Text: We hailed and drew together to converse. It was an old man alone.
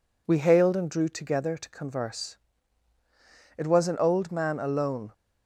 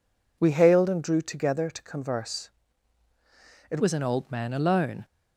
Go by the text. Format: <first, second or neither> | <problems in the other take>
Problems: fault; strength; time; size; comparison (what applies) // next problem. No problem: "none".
first | changes voice at "was"; from 3.7 s on; 1.3 s long